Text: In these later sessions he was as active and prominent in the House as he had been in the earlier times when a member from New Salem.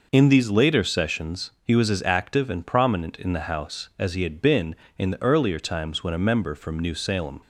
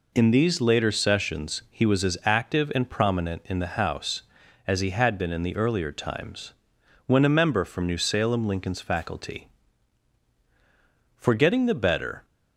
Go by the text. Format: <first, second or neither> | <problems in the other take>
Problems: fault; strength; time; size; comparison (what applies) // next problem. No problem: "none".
first | pauses between "times" and "when"; noticeable; at 6.5 s; 0.54 s long // goes on to say "Lincoln's faculty for getting the better"; strong; from 8.4 s on; 3.7 s long